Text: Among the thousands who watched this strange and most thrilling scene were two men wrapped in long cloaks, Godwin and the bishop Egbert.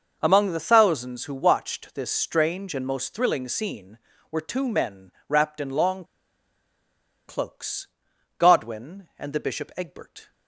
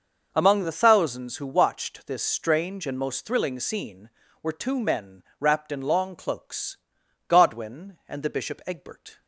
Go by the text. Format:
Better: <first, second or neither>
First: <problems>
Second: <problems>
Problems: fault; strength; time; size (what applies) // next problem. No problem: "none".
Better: second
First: pauses between "men" and "wrapped"; slight; at 5.1 s; 0.16 s long // pauses between "long" and "cloaks"; strong; at 6.0 s; 1.2 s long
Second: pauses between "men" and "wrapped"; slight; at 5.2 s; 0.16 s long